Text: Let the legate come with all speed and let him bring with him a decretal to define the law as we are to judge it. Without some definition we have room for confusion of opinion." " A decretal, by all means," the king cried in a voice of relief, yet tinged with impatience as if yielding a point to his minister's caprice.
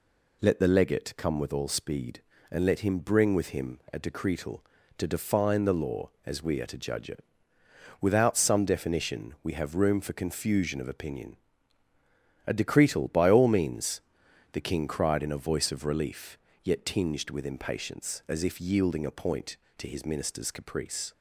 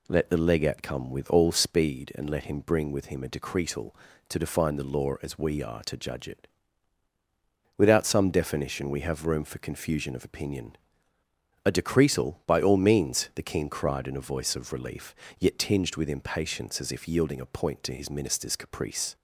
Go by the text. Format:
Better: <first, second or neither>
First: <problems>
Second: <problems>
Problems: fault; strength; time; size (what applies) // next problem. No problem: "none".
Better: neither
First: none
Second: none